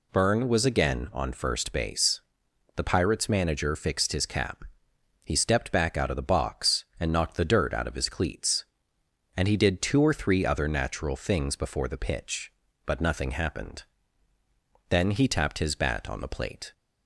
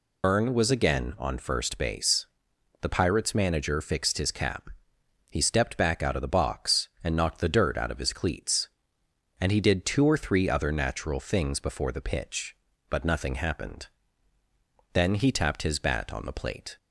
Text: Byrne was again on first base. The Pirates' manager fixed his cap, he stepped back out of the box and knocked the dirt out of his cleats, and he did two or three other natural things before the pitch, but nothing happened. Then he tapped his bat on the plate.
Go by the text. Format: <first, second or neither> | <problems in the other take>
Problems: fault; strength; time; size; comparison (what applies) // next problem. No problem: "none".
first | loses the start of "Byrne"; at 0.2 s; 70 ms